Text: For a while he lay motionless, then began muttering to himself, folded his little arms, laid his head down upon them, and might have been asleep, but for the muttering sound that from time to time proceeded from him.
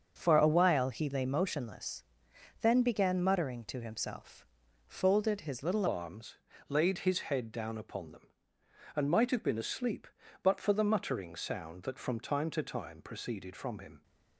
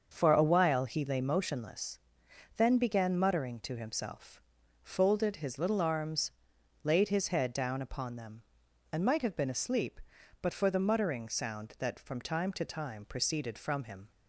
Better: second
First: starts louder than the rest; until 1.1 s; 6.5 dB // changes voice at "arms"; from 5.8 s on; 8.2 s long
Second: starts louder than the rest; until 1.1 s; 6.5 dB

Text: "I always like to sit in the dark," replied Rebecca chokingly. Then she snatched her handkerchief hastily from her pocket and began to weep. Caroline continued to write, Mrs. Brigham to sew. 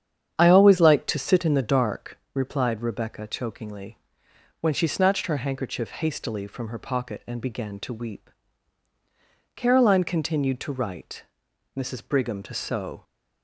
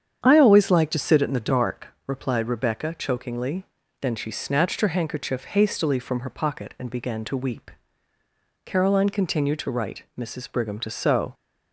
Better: second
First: starts louder than the rest; strong; until 1.4 s; 8.5 dB // says "When" for "Then"; at 4.6 s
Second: starts louder than the rest; strong; until 1.2 s; 8 dB

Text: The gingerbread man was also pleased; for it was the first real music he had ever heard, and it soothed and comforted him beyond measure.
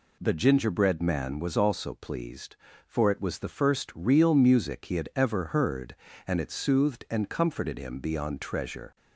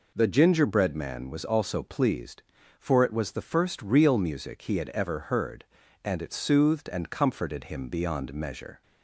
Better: second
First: says "treasure" for "measure"; at 8.4 s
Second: none

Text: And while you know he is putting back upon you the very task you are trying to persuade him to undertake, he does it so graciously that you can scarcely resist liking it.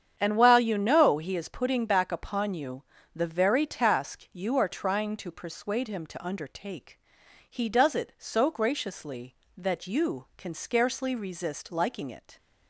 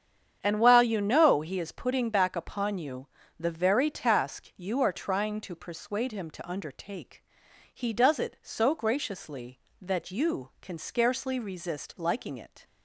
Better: neither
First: starts louder than the rest; strong; until 1.1 s; 8 dB // pauses between "you" and "the"; slight; at 2.8 s; 0.30 s long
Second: starts louder than the rest; strong; until 1.4 s; 8 dB // pauses between "you" and "the"; slight; at 3.0 s; 0.30 s long

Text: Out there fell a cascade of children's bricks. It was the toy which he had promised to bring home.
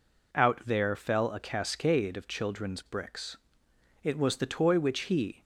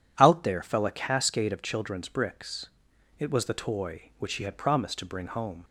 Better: second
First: stops before "had promised to bring home"; at 5.4 s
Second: none

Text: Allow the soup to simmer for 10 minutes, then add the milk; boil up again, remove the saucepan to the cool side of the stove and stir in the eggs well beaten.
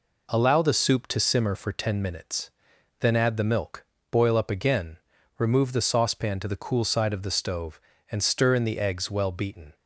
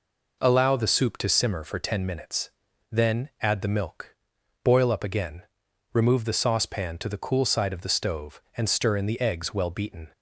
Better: neither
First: none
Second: none

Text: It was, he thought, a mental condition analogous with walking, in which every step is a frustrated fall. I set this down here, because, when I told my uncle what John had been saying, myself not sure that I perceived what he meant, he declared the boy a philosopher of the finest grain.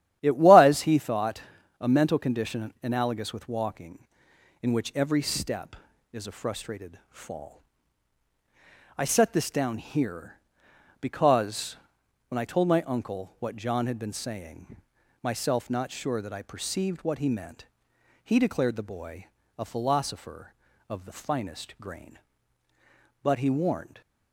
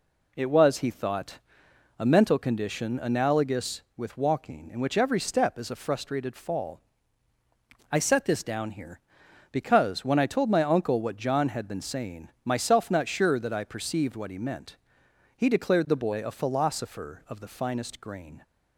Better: second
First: starts louder than the rest; strong; until 1.2 s; 11.5 dB // pauses between "boy" and "a"; slight; at 19.2 s; 0.32 s long // goes on to say "But he warned"; noticeable; from 23.2 s on; 0.78 s long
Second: none

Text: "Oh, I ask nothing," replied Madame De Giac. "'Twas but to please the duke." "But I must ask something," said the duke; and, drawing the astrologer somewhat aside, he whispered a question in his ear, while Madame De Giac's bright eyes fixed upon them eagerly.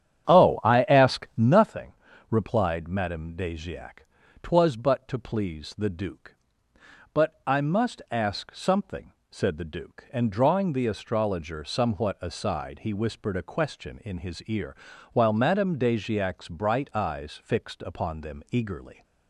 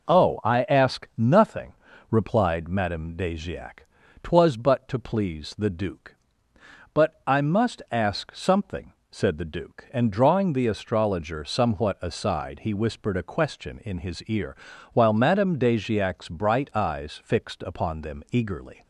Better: second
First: starts louder than the rest; strong; until 1.7 s; 10 dB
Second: none

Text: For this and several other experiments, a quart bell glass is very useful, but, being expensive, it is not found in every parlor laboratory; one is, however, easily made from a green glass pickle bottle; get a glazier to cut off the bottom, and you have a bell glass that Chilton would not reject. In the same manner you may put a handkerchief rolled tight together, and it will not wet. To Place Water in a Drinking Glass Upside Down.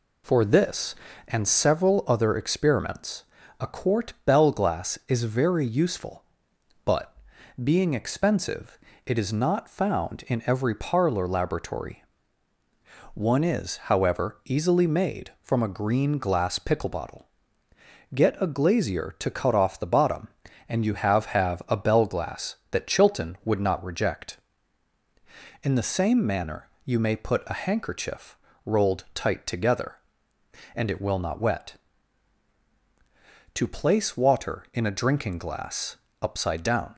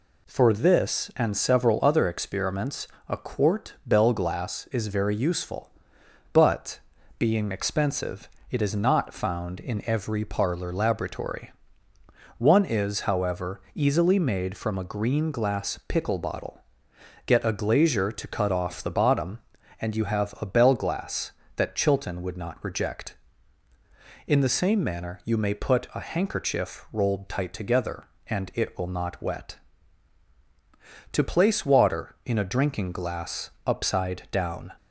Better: second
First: says "have" twice; at 21.3 s // pauses between "manner" and "you"; slight; at 26.6 s; 0.16 s long // pauses between "handkerchief" and "rolled"; slight; at 28.3 s; 0.30 s long // pauses between "Glass" and "Upside"; slight; at 35.9 s; 0.26 s long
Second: pauses between "Glass" and "Upside"; slight; at 33.5 s; 0.16 s long

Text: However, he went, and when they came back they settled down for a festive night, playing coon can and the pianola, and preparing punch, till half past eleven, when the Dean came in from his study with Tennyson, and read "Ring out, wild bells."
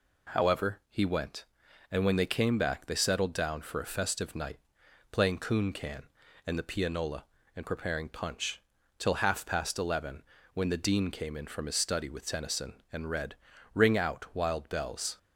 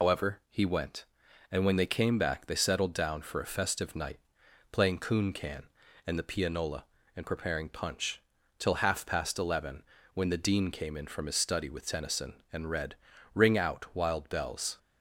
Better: first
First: pauses between "read" and "Ring"; at 13.3 s; 0.38 s long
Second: loses the start of "However"; at 0.0 s; 140 ms // pauses between "read" and "Ring"; at 12.9 s; 0.38 s long

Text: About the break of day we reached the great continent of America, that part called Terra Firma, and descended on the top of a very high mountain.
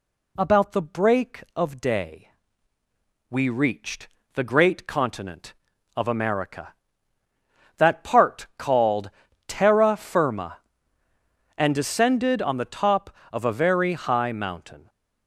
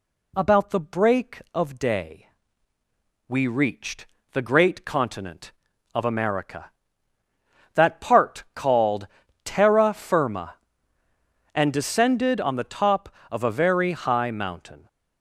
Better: neither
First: pauses between "day" and "we"; at 2.2 s; 1.0 s long // pauses between "reached" and "the"; slight; at 4.0 s; 0.28 s long // pauses between "called" and "Terra"; at 9.0 s; 0.38 s long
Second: pauses between "day" and "we"; at 2.2 s; 1.0 s long // pauses between "reached" and "the"; slight; at 4.0 s; 0.28 s long // pauses between "called" and "Terra"; at 9.0 s; 0.38 s long

